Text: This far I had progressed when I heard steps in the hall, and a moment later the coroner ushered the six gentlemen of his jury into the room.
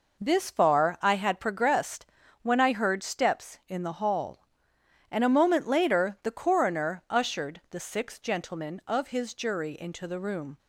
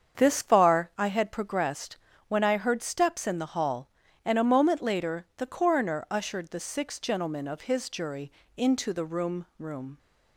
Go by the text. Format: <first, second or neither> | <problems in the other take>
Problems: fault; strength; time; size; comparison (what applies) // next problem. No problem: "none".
first | starts louder than the rest; strong; until 1.2 s; 7.5 dB // pauses between "progressed" and "when"; slight; at 1.9 s; 0.30 s long; also in the first // pauses between "jury" and "into"; slight; at 8.3 s; 0.24 s long // says "room" twice; at 9.5 s